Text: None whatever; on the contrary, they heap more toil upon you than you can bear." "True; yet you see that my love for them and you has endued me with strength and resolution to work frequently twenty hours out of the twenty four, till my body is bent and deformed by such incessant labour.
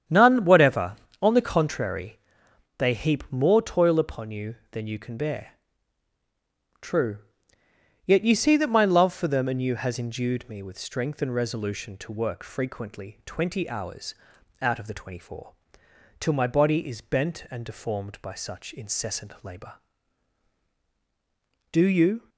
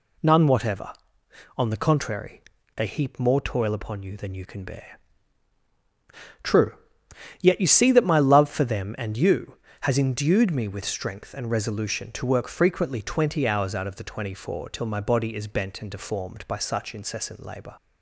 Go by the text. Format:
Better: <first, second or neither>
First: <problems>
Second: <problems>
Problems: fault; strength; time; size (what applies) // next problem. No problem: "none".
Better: second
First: starts louder than the rest; strong; until 1.3 s; 9 dB // pauses between "hours" and "out"; noticeable; at 14.1 s; 0.46 s long // goes on to say "Do you"; from 21.7 s on; 0.56 s long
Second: none